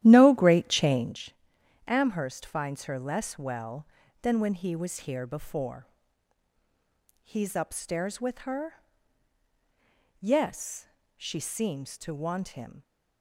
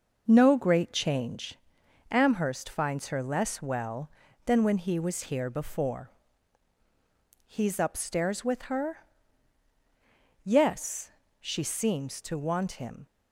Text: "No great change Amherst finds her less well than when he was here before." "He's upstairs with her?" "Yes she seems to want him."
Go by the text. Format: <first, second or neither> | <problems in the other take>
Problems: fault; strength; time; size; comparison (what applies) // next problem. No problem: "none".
second | starts louder than the rest; strong; until 1.2 s; 12.5 dB // pauses between "change" and "Amherst"; noticeable; at 1.3 s; 0.54 s long; noticeable in the second // pauses between "Yes" and "she"; slight; at 10.8 s; 0.28 s long; slight in the second